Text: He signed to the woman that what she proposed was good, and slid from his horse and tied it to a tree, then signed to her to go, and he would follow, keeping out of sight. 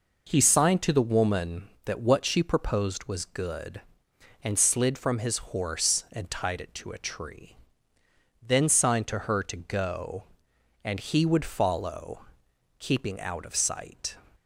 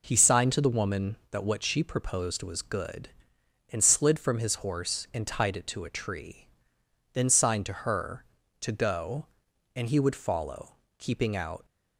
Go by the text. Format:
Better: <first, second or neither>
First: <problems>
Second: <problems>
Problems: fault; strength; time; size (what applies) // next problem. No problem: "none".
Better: first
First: none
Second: stops before "of sight"; at 11.6 s